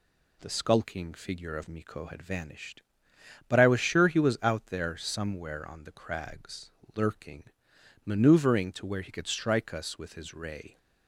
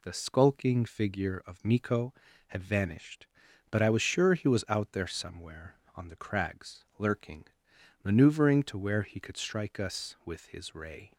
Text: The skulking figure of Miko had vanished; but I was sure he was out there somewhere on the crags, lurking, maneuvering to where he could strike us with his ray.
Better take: neither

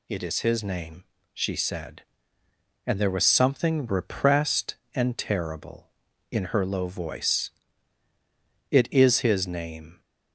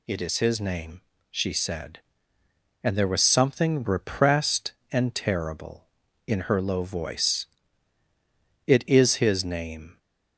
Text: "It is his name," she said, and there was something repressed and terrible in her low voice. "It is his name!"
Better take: neither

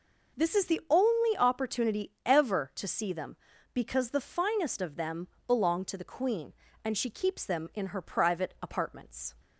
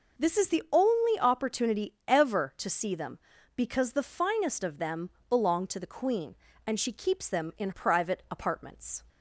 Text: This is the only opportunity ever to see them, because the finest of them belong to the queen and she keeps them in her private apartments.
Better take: first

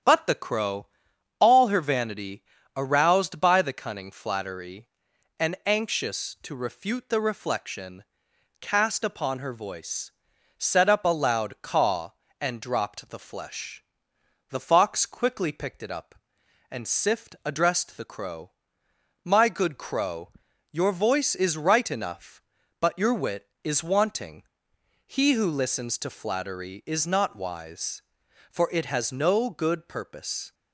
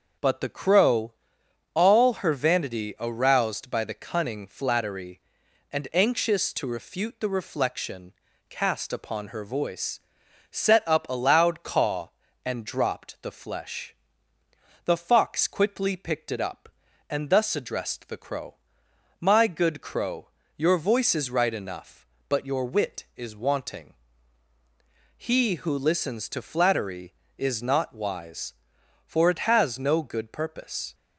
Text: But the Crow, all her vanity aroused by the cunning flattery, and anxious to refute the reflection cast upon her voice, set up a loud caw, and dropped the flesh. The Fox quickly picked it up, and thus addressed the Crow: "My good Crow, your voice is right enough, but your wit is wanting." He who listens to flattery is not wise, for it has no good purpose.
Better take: second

